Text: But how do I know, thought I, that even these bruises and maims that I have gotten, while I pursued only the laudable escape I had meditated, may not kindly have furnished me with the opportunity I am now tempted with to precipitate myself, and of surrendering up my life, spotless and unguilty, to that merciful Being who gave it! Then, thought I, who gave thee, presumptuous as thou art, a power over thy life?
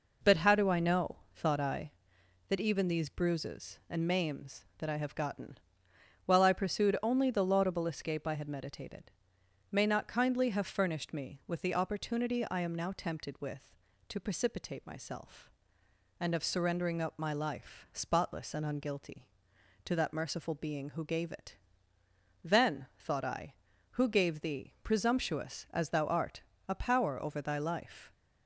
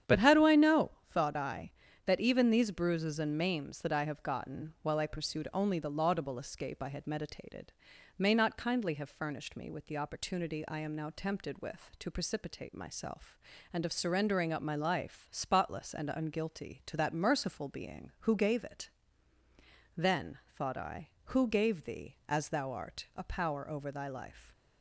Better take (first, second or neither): first